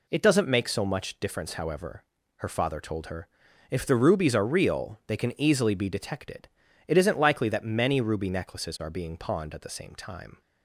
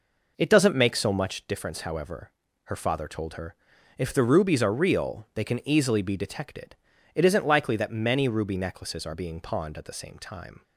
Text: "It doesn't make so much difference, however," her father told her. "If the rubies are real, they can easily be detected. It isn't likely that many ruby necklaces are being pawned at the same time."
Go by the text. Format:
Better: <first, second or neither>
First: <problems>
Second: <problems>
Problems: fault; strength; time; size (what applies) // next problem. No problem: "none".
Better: first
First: none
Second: starts louder than the rest; noticeable; until 1.3 s; 5 dB